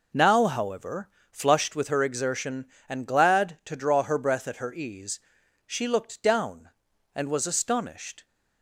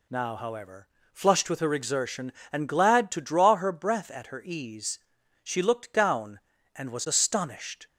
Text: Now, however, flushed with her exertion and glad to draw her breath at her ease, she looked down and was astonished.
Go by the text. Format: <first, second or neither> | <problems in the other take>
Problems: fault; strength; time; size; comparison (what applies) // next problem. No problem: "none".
neither | none